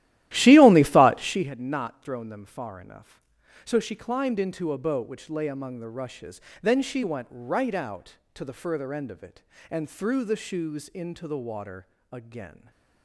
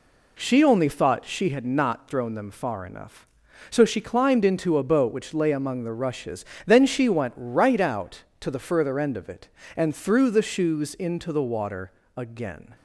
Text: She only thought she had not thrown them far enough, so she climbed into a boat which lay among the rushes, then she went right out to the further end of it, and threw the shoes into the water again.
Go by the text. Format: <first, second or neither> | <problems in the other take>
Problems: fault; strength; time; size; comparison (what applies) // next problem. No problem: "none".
second | starts louder than the rest; strong; until 1.5 s; 14.5 dB // pauses between "water" and "again"; slight; at 11.8 s; 0.26 s long; slight in the second